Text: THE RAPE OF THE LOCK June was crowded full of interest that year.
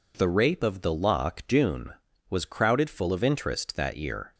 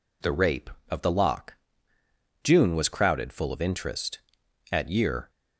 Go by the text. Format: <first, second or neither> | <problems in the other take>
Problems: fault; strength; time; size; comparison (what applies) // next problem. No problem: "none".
first | pauses between "LOCK" and "June"; noticeable; at 1.5 s; 0.90 s long // says "at" for "that"; at 4.6 s